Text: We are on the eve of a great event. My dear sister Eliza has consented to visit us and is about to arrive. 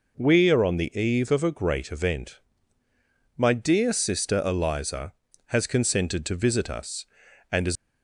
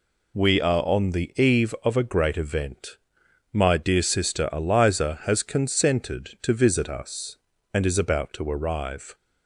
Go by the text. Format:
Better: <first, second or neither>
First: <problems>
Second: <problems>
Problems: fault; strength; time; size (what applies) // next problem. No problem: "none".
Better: second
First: stops before "about to arrive"; at 7.7 s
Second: none